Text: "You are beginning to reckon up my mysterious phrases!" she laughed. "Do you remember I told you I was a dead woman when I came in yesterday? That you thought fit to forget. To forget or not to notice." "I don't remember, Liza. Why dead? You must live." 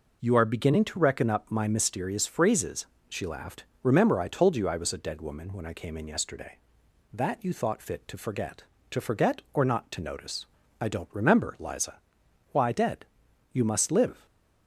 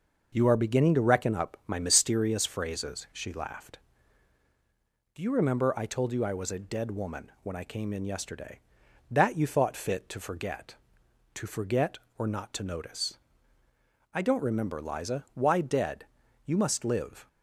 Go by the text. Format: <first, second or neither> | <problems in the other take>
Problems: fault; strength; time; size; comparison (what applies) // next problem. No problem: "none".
second | skips "Do you"; at 3.7 s